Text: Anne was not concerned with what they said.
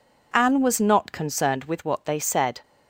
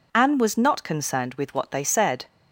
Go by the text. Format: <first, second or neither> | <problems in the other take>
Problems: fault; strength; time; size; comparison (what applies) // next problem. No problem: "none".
neither | none